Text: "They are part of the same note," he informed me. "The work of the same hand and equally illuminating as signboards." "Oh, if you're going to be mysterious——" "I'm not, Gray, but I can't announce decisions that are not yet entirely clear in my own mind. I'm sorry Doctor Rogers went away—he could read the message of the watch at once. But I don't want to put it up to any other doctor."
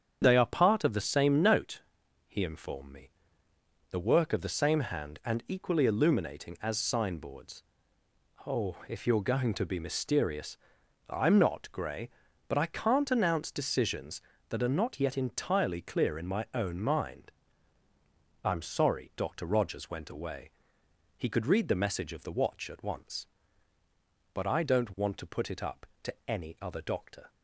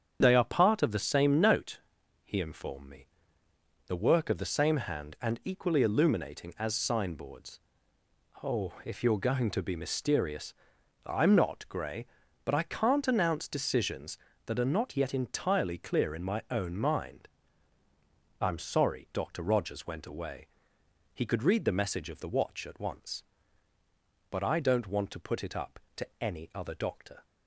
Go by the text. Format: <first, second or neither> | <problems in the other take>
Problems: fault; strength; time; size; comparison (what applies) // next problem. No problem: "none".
neither | starts louder than the rest; strong; the same in both